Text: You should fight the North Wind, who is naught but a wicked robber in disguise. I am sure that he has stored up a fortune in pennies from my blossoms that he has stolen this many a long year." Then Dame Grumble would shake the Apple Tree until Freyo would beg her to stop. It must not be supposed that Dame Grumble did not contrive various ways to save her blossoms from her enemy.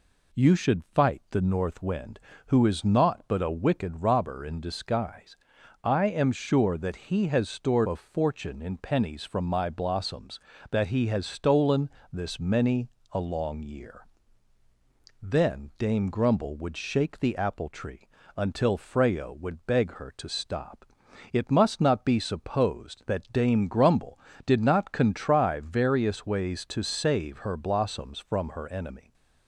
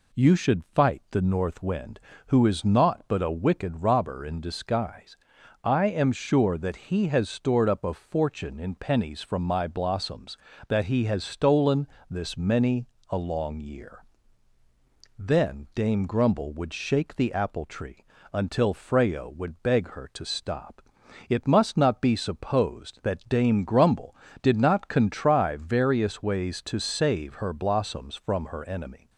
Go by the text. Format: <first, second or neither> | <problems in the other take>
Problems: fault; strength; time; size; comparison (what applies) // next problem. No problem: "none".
second | skips "up"; at 7.8 s // pauses between "stolen" and "this"; slight; at 11.8 s; 0.22 s long; slight in the second // pauses between "many" and "a"; slight; at 12.8 s; 0.24 s long; slight in the second // pauses between "Tree" and "until"; slight; at 18.0 s; 0.26 s long; slight in the second